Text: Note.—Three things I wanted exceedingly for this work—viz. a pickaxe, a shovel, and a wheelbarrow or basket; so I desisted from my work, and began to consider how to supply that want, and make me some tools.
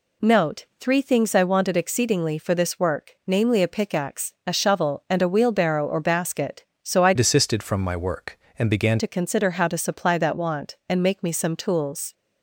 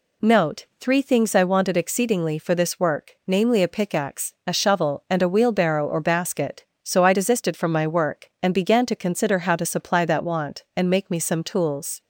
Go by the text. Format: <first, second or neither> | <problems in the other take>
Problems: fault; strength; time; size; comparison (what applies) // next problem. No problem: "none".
second | changes voice from "desisted" to "began"; from 7.1 to 9.0 s; 1.9 s long